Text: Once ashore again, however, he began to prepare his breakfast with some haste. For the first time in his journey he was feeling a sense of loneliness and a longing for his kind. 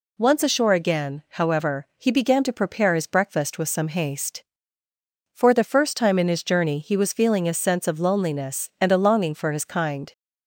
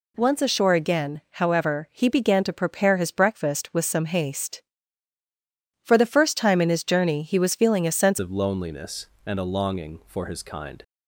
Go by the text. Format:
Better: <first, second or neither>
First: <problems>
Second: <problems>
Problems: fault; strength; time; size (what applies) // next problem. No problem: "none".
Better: first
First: none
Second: changes voice at "of"; from 8.1 s on; 2.7 s long